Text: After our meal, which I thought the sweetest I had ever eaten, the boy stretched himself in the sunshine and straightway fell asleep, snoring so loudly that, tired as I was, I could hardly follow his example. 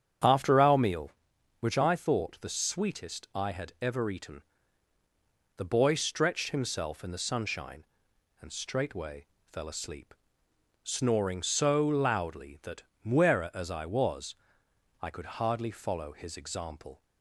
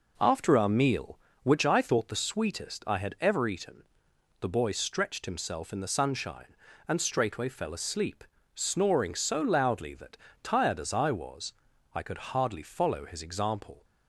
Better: second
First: starts louder than the rest; strong; until 1.7 s; 8.5 dB // pauses between "straightway" and "fell"; slight; at 9.2 s; 0.26 s long // says "muera" for "tired"; at 13.0 s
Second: none

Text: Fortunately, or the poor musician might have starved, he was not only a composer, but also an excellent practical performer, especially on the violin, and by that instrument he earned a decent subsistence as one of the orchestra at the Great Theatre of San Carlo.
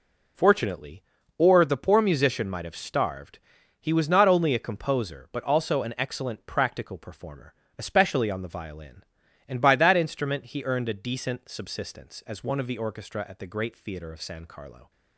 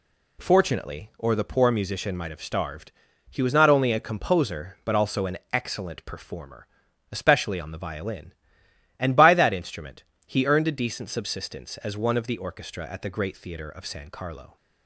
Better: first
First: none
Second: skips "practical"; at 6.0 s // pauses between "instrument" and "he"; slight; at 10.0 s; 0.24 s long

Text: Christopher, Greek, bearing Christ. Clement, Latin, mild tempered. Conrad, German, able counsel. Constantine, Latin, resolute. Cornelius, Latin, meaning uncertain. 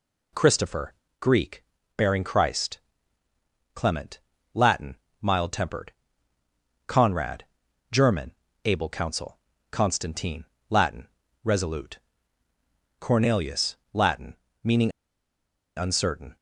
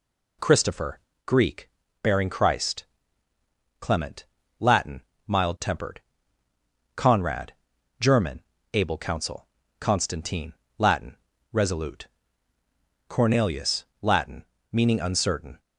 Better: second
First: pauses between "meaning" and "uncertain"; noticeable; at 14.9 s; 0.85 s long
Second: none

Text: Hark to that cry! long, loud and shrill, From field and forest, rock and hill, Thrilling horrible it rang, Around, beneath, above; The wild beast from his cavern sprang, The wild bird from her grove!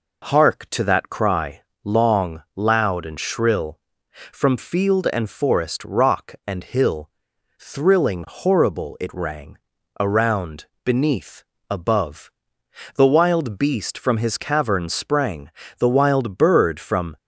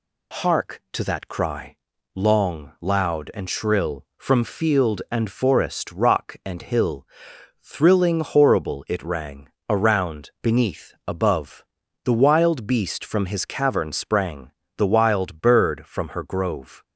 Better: second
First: stops before "her grove"; at 17.1 s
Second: none

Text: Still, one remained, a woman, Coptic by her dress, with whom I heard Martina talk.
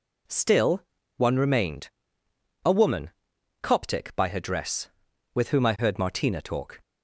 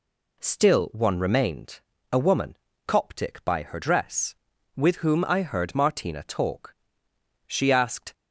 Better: first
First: none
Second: goes on to say "She asked"; noticeable; from 7.4 s on; 0.66 s long

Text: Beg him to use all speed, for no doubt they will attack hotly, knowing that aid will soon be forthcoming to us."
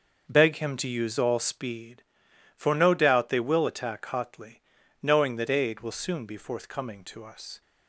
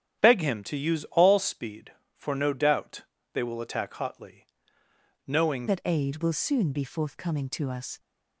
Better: first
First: starts louder than the rest; noticeable; until 1.2 s; 6 dB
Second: starts louder than the rest; strong; until 1.2 s; 9.5 dB // pauses between "doubt" and "they"; slight; at 3.0 s; 0.32 s long // changes voice at "that"; from 5.6 s on; 2.3 s long

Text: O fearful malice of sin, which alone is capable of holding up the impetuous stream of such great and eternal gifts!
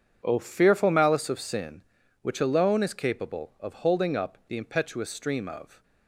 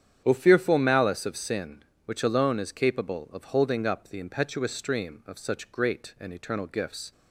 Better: second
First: starts louder than the rest; strong; until 1.2 s; 8 dB // stops before "such great and eternal gifts"; at 5.8 s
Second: starts louder than the rest; strong; until 1.2 s; 9 dB

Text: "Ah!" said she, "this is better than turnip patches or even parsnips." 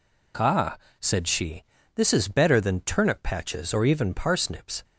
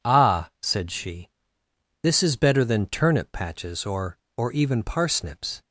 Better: first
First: none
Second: says "or" twice; at 4.3 s

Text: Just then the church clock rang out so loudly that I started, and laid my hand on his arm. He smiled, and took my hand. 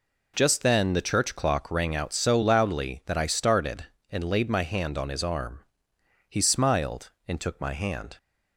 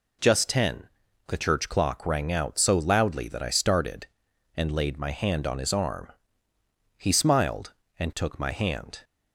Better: first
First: none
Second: says "ten" for "then"; at 0.4 s

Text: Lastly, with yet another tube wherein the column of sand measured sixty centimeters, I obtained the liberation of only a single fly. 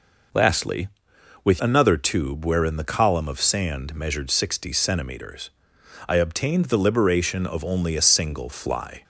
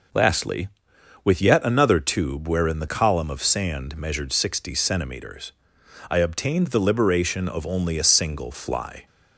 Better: second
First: skips "yet"; at 1.6 s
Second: none

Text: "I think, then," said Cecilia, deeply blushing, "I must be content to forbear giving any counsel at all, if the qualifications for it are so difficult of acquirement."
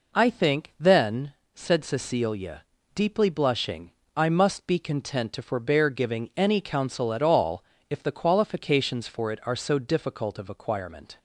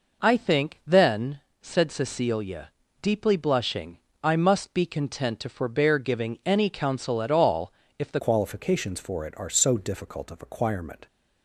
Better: first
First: none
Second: changes voice at "qualifications"; from 8.1 s on; 2.9 s long

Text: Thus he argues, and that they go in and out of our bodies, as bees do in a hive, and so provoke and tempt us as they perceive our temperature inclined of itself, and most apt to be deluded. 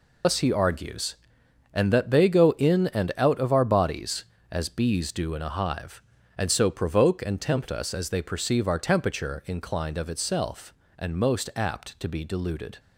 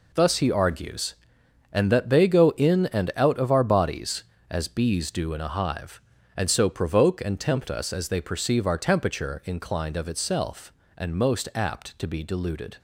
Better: second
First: loses the start of "Thus"; at 0.2 s; 95 ms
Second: none

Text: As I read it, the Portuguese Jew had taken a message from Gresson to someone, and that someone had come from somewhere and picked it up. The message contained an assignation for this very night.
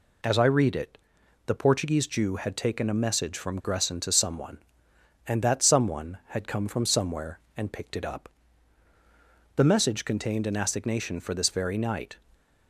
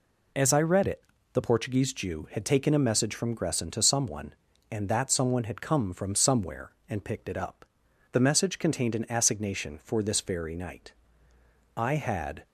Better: first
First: none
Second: goes on to say "I had"; noticeable; from 11.7 s on; 0.68 s long

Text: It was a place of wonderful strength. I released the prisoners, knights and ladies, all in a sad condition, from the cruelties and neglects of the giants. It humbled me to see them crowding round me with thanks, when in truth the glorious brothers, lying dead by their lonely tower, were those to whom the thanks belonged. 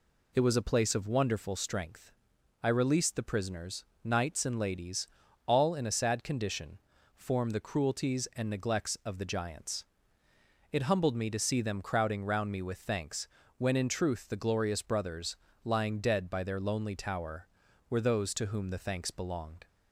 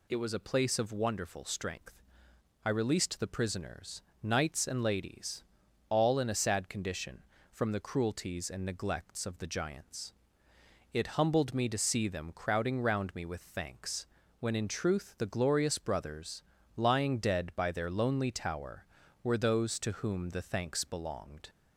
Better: second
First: says "form" for "from"; at 7.1 s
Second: none

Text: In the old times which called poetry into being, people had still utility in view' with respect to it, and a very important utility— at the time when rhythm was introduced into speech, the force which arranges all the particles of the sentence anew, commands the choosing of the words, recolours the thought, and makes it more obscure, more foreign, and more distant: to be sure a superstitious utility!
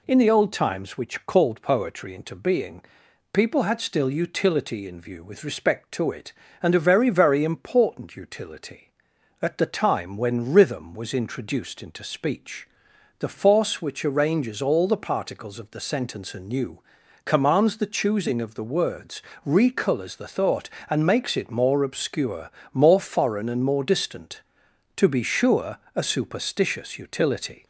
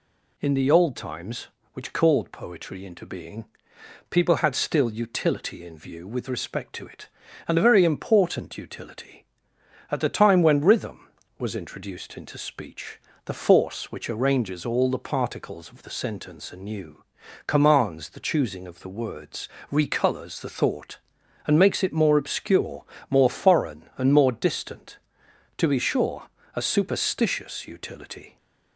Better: second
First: says "very" twice; at 7.0 s // pauses between "sure" and "a"; slight; at 25.7 s; 0.18 s long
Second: pauses between "sure" and "a"; slight; at 26.2 s; 0.26 s long

